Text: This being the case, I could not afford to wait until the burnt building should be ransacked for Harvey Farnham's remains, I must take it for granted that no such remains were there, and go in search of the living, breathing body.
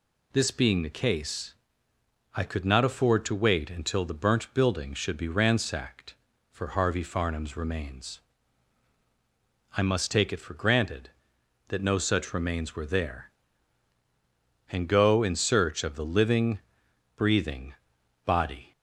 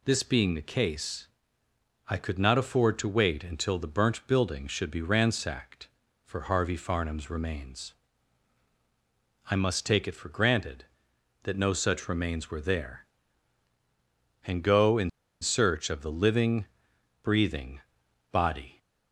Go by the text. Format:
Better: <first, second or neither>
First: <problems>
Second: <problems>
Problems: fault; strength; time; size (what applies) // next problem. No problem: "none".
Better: first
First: pauses between "breathing" and "body"; noticeable; at 17.7 s; 0.50 s long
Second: pauses between "in" and "search"; slight; at 15.0 s; 0.32 s long // pauses between "breathing" and "body"; noticeable; at 17.7 s; 0.50 s long